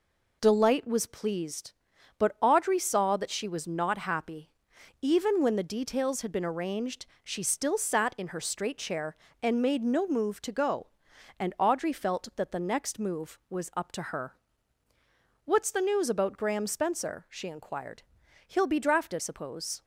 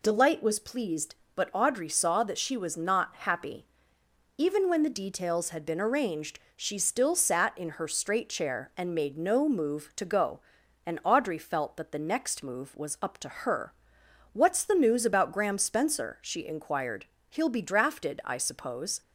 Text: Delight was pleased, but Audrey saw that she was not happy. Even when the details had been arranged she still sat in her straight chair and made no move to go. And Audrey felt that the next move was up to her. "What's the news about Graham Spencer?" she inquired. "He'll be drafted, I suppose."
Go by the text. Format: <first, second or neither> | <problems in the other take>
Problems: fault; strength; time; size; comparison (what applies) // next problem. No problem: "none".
second | pauses between "arranged" and "she"; slight; at 7.0 s; 0.20 s long; slight in the second // skips "I"; at 19.1 s